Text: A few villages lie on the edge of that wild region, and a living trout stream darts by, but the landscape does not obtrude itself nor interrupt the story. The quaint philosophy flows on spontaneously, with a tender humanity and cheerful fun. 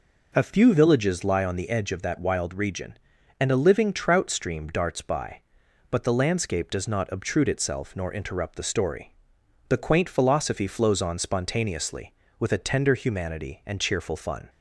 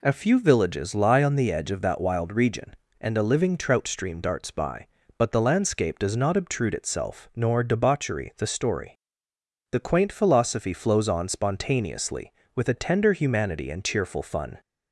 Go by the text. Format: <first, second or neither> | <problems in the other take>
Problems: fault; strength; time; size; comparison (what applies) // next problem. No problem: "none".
first | says "debauchery" for "interrupt"; at 7.6 s